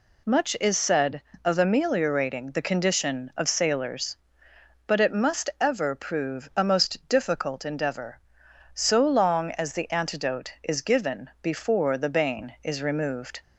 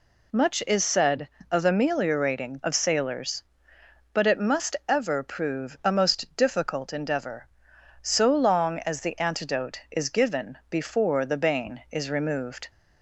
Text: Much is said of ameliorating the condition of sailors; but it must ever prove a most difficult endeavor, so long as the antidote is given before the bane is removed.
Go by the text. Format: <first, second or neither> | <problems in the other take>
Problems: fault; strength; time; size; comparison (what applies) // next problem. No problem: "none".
first | skips "the condition"; at 2.6 s